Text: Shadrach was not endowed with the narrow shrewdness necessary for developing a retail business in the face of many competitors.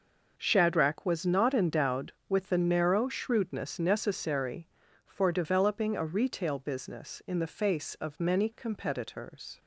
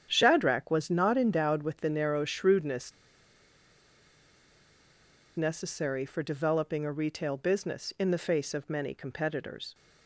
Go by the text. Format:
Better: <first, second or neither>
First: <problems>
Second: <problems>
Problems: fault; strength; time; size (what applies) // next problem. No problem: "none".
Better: first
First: none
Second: starts louder than the rest; strong; until 1.1 s; 9 dB // pauses between "shrewdness" and "necessary"; strong; at 2.9 s; 2.4 s long